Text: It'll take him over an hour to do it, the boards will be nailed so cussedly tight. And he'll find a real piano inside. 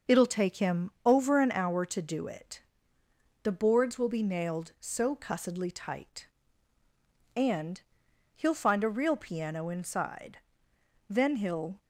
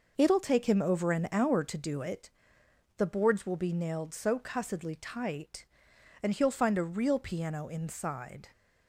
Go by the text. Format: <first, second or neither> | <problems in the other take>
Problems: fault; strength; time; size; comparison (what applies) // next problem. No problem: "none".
second | starts louder than the rest; until 1.2 s; 6 dB // pauses between "him" and "over"; slight; at 0.8 s; 0.16 s long // pauses between "And" and "he'll"; noticeable; at 7.8 s; 0.54 s long // goes on to say "Then he'll"; noticeable; from 11.1 s on; 0.72 s long